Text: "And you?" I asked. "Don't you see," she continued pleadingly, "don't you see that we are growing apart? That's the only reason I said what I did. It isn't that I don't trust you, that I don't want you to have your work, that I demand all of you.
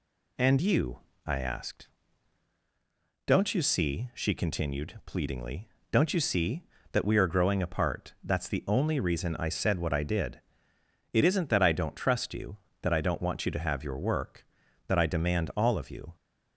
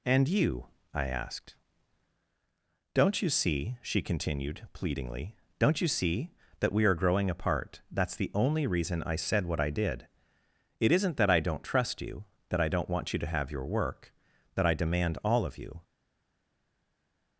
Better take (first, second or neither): first